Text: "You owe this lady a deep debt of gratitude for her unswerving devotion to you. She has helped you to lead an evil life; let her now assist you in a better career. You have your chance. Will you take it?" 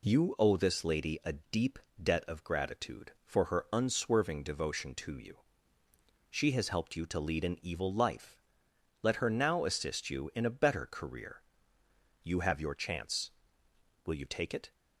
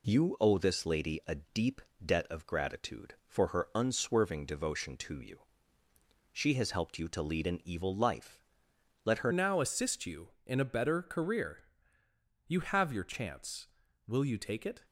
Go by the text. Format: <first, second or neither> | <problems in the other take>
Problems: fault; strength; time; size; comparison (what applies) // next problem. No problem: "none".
first | pauses between "deep" and "debt"; slight; at 1.8 s; 0.24 s long; slight in the first // changes voice at "now"; from 9.3 s on; 5.5 s long